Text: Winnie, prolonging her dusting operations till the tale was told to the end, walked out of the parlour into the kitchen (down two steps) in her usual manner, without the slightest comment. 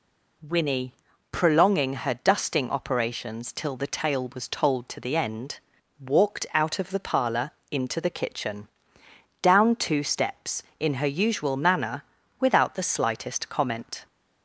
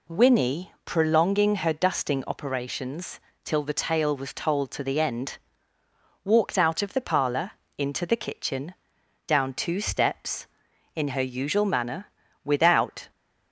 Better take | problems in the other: first | pauses between "operations" and "till"; slight; at 3.1 s; 0.24 s long // pauses between "parlour" and "into"; slight; at 7.4 s; 0.26 s long; slight in the first // stops before "the slightest comment"; at 13.0 s

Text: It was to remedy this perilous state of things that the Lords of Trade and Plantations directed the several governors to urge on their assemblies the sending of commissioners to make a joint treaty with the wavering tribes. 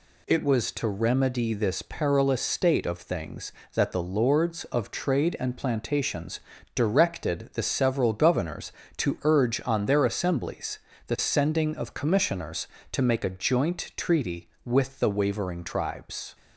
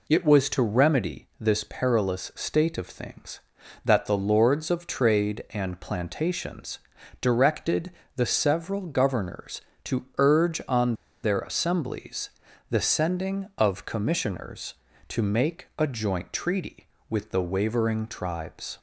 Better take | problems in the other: first | pauses between "Plantations" and "directed"; at 6.7 s; 0.42 s long; slight in the first // pauses between "directed" and "the"; slight; at 7.9 s; 0.26 s long // pauses between "on" and "their"; slight; at 10.9 s; 0.28 s long // pauses between "assemblies" and "the"; at 12.2 s; 0.40 s long; slight in the first

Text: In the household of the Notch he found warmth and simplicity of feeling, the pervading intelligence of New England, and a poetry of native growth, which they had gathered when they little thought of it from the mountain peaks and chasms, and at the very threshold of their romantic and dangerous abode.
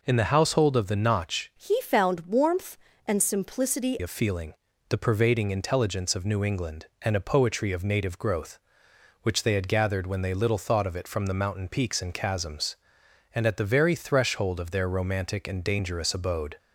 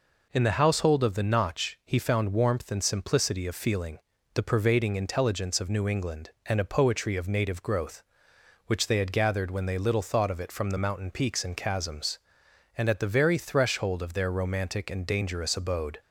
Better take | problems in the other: second | changes voice from "he" to "simplicity"; from 1.5 to 3.9 s; 2.4 s long

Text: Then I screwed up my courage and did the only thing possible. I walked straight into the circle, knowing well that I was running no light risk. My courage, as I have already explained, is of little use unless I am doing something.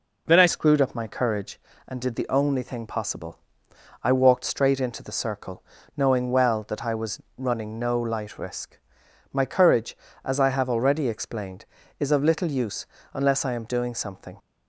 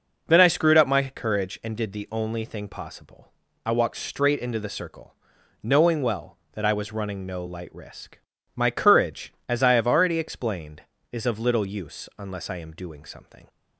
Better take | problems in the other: second | changes voice at "screwed"; from 0.4 s on; 13.9 s long // pauses between "was" and "running"; slight; at 7.2 s; 0.16 s long // pauses between "use" and "unless"; slight; at 12.8 s; 0.28 s long

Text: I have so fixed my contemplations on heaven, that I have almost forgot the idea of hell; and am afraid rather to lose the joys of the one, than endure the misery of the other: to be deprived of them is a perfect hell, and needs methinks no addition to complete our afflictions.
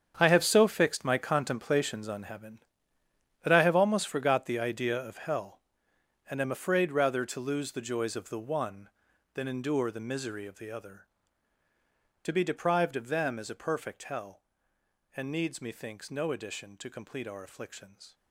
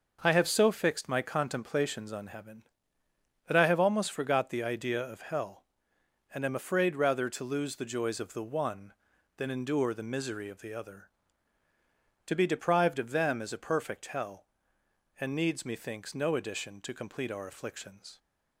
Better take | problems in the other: second | gets quieter; strong; throughout; 13.5 dB // starts louder than the rest; strong; until 1.1 s; 8 dB; noticeable in the second

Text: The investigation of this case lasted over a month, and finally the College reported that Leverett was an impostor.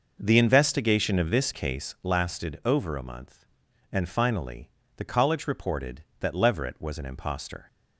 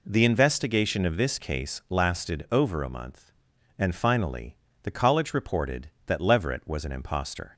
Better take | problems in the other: second | starts louder than the rest; noticeable; until 1.8 s; 6 dB // pauses between "finally" and "the"; slight; at 4.7 s; 0.24 s long; slight in the second

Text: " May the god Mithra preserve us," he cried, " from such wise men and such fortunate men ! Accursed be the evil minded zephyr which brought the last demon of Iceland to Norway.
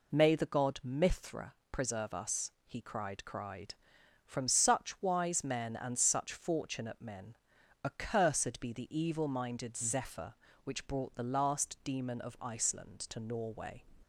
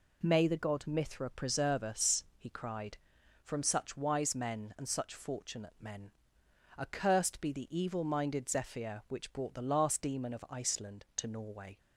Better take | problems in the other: second | pauses between "Mithra" and "preserve"; slight; at 1.5 s; 0.18 s long // says "cried" twice; at 3.2 s

